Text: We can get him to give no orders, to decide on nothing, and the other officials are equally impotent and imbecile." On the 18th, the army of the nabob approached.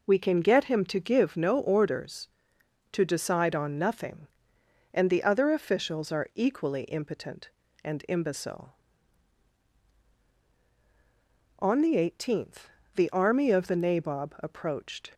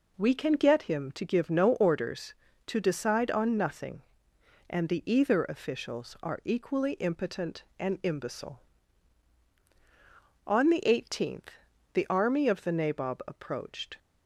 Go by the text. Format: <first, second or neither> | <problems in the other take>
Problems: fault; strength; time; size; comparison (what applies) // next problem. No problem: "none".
first | says "either" for "other"; at 5.1 s